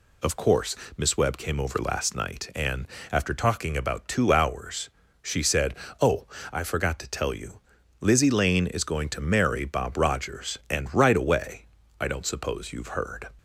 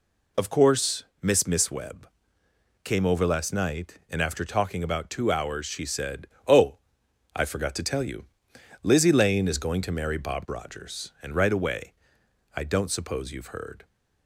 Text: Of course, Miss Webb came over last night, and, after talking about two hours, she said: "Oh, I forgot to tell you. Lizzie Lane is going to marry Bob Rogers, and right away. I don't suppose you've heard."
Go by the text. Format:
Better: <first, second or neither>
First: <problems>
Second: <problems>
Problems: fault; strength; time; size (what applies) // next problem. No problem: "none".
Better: first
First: none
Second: says "Miss" twice; at 1.4 s // pauses between "Webb" and "came"; noticeable; at 2.0 s; 0.74 s long